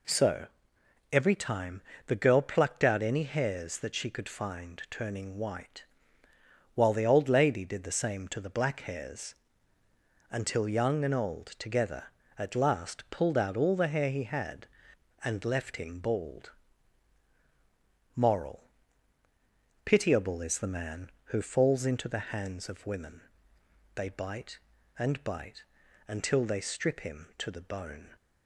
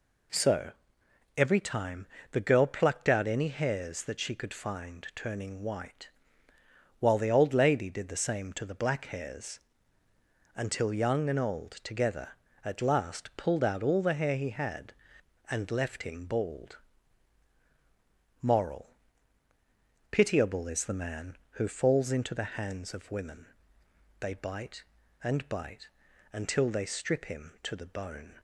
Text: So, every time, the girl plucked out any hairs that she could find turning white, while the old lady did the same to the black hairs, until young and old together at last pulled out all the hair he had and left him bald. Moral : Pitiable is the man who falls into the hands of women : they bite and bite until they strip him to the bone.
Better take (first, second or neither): neither